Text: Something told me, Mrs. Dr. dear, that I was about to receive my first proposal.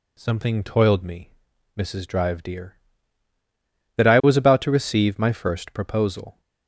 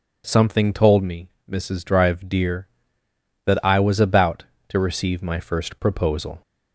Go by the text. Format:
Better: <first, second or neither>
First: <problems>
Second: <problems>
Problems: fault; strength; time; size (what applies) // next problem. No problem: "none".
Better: second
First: says "toiled" for "told"; at 0.6 s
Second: none